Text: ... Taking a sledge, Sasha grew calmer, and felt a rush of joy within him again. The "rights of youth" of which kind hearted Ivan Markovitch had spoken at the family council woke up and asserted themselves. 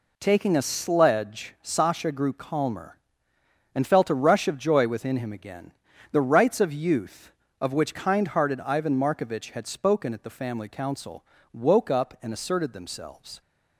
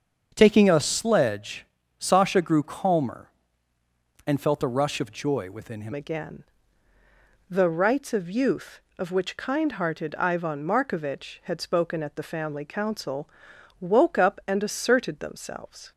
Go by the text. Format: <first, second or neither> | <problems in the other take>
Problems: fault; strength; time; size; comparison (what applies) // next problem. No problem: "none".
first | starts louder than the rest; until 1.3 s; 7 dB // changes voice at "again"; from 5.9 s on; 10.0 s long // pauses between "council" and "woke"; noticeable; at 13.2 s; 0.52 s long; slight in the first